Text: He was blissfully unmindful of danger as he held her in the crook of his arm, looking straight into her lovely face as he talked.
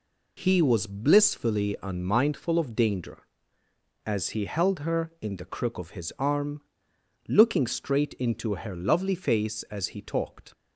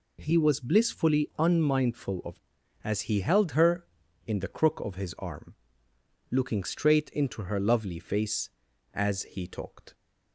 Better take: first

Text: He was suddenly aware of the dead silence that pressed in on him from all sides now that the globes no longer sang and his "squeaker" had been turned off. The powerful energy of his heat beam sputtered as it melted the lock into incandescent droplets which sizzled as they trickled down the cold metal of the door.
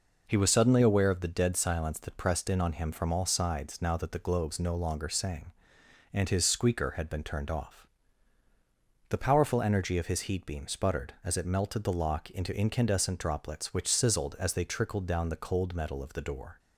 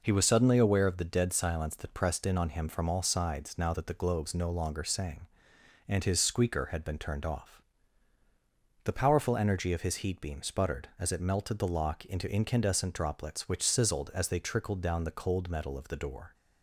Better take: neither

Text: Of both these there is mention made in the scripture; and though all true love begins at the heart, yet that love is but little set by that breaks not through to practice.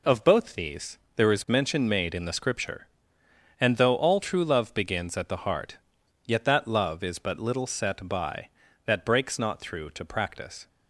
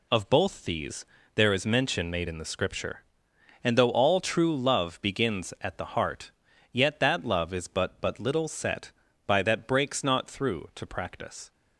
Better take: first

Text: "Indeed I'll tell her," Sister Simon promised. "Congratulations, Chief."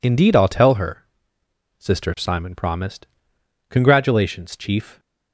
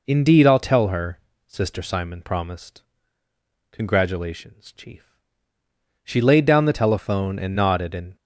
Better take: first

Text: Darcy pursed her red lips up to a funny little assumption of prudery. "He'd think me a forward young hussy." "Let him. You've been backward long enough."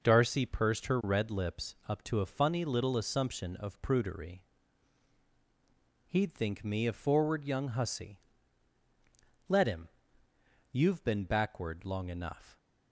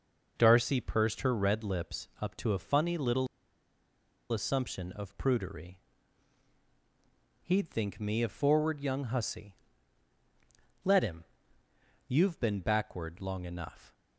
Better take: first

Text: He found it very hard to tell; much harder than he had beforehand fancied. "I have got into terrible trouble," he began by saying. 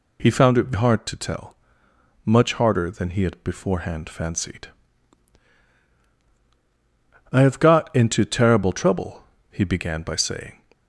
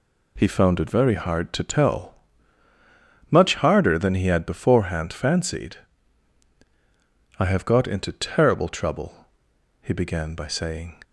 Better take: second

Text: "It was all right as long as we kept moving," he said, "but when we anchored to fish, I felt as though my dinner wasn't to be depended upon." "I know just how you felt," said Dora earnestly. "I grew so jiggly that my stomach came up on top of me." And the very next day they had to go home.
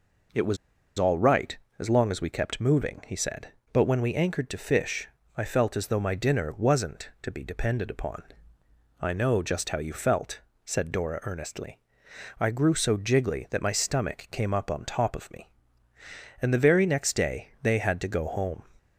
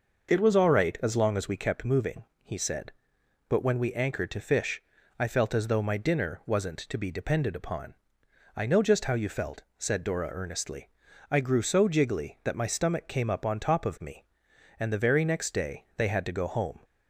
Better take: second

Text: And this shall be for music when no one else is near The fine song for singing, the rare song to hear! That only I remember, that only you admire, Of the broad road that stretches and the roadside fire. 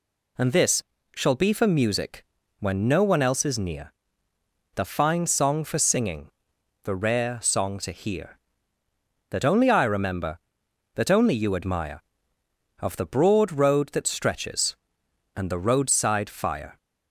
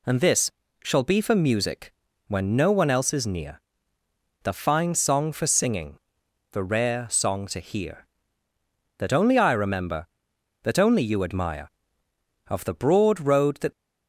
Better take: first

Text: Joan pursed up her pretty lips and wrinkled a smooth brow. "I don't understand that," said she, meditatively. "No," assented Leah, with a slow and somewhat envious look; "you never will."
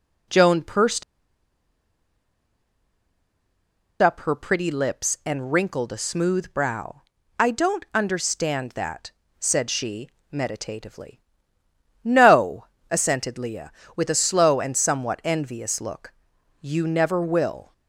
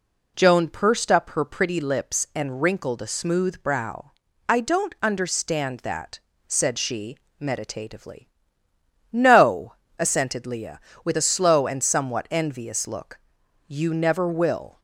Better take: second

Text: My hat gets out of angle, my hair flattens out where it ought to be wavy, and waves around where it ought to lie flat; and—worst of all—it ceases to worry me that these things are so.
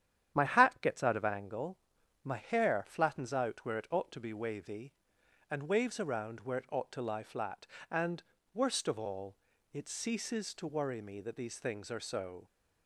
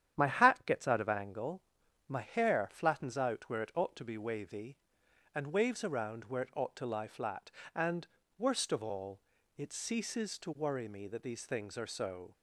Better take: neither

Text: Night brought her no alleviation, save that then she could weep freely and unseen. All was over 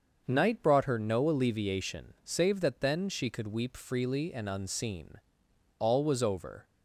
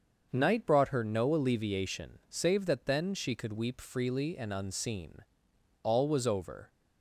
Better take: neither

